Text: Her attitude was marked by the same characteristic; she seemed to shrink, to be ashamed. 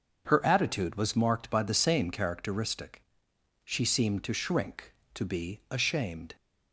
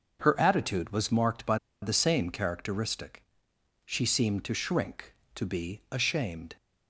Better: first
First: starts louder than the rest; until 1.2 s; 6.5 dB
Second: starts louder than the rest; noticeable; until 1.2 s; 6 dB // pauses between "by" and "the"; slight; at 1.5 s; 0.25 s long

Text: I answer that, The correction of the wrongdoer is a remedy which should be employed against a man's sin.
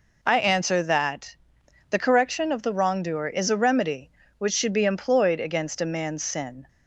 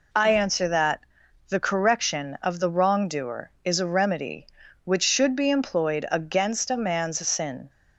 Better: neither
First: none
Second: none

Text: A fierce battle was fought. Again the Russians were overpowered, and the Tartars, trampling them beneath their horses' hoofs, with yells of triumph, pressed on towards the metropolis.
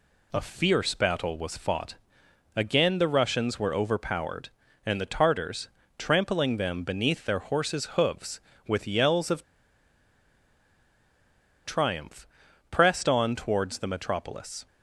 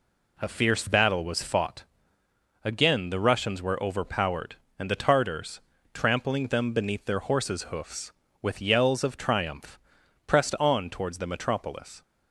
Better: second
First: pauses between "of" and "triumph"; strong; at 9.4 s; 2.2 s long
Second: none

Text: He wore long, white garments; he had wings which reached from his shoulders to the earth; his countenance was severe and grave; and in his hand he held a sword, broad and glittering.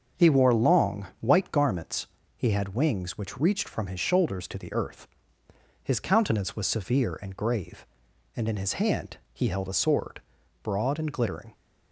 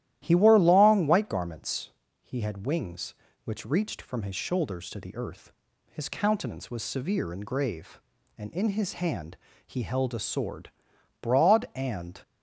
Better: first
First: starts louder than the rest; noticeable; until 1.2 s; 6 dB // pauses between "hand" and "he"; slight; at 9.1 s; 0.16 s long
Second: starts louder than the rest; strong; until 1.2 s; 13 dB // pauses between "hand" and "he"; slight; at 9.3 s; 0.32 s long // stops before "glittering"; at 12.2 s

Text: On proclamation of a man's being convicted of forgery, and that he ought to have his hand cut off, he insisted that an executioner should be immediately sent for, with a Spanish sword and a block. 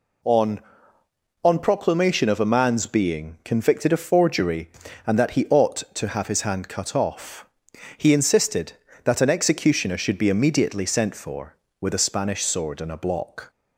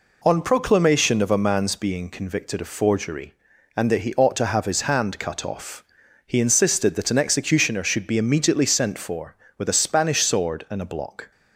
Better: second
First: says "On" twice; at 1.4 s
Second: none

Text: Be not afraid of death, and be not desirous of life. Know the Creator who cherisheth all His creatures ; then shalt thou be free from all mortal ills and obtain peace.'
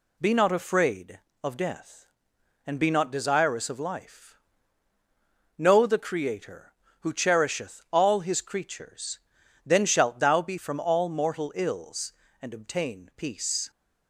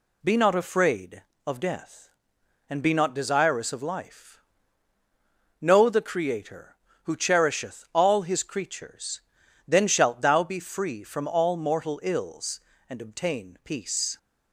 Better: second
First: skips "free"; at 10.5 s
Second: none

